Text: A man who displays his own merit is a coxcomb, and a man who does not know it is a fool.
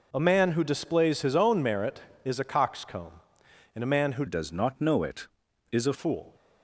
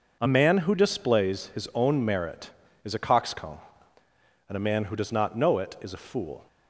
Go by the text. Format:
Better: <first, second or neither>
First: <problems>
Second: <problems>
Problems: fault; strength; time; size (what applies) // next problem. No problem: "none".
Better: second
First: changes voice from "does" to "a"; from 4.2 to 5.9 s; 1.7 s long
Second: none